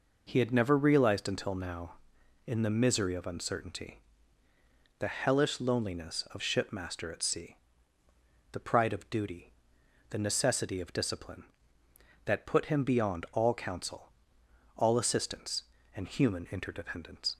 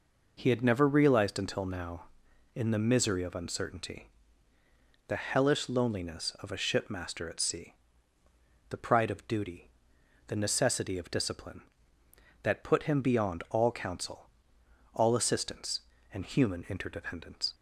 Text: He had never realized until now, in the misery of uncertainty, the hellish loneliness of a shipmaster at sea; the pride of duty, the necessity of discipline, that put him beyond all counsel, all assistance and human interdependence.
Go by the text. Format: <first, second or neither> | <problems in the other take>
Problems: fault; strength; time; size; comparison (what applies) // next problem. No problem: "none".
second | skips "a"; at 6.4 s